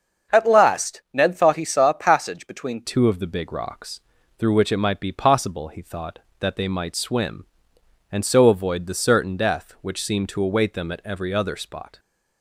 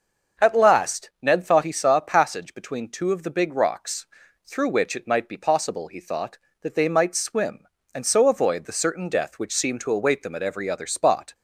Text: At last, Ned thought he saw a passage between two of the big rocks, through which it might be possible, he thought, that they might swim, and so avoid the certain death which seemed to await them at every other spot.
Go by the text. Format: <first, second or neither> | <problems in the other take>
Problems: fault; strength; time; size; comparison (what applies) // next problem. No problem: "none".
second | starts louder than the rest; until 1.4 s; 6.5 dB; noticeable in the second // changes voice at "two"; from 2.8 s on; 9.1 s long